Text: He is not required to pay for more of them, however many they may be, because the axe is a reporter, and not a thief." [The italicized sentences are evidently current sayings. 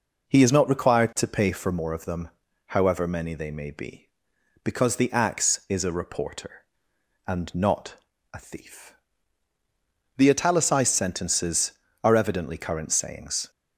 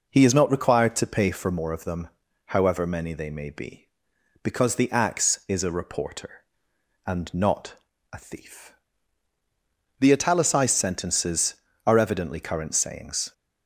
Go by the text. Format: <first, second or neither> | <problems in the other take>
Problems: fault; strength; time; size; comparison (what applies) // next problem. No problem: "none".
neither | pauses between "not" and "a"; slight; the same in both